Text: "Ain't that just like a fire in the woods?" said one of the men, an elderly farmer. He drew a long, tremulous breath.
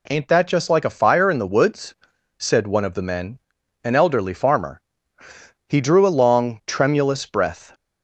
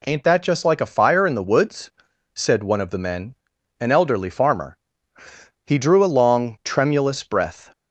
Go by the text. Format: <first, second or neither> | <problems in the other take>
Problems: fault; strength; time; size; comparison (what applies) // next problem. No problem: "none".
neither | none